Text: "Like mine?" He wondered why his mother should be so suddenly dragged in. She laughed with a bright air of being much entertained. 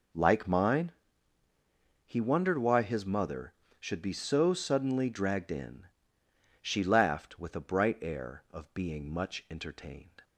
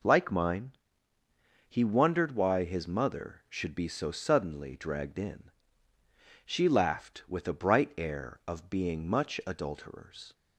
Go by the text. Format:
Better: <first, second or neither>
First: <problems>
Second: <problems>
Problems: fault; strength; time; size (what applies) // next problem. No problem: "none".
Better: first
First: none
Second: says "adulterers" for "entertained"; at 9.4 s